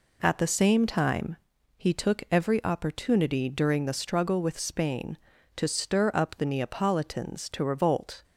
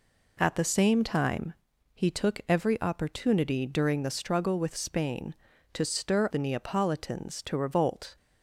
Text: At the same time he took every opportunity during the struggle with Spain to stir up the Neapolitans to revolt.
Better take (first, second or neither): first